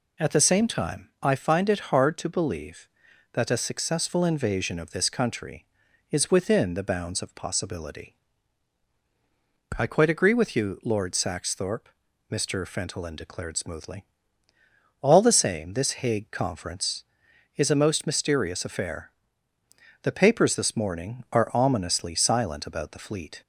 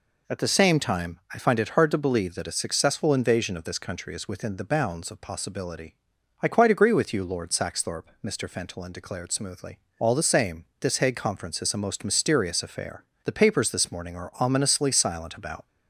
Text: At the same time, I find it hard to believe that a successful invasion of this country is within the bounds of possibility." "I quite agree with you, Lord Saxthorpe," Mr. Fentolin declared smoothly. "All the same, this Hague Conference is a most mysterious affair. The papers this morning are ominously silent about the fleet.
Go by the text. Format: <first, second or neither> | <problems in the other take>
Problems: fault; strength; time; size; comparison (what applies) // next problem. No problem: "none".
first | stops before "the fleet"; at 15.6 s